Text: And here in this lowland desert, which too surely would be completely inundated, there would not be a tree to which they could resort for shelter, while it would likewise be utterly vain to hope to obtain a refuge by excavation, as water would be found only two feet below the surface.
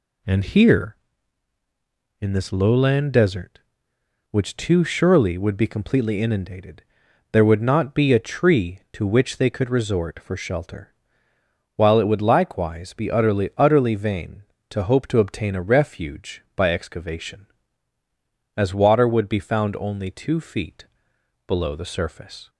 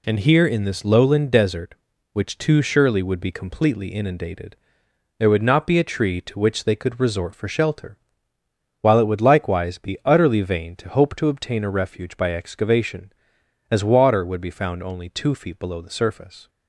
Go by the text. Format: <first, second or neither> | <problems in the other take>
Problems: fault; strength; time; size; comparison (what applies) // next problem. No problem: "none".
second | says "utterly" twice; at 13.5 s // pauses between "feet" and "below"; noticeable; at 20.8 s; 0.62 s long